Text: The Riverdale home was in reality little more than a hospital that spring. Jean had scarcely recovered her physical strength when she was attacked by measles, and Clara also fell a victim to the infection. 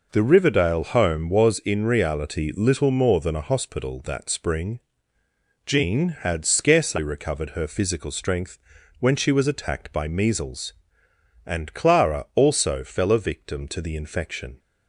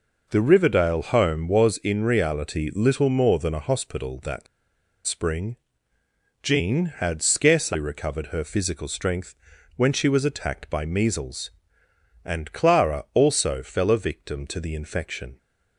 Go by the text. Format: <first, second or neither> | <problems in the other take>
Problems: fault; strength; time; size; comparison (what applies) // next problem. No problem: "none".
first | pauses between "that" and "spring"; noticeable; at 4.4 s; 0.61 s long // pauses between "strength" and "when"; at 9.3 s; 0.44 s long; also in the first